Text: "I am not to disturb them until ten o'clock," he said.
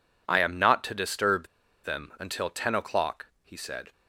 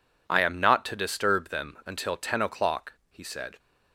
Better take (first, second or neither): second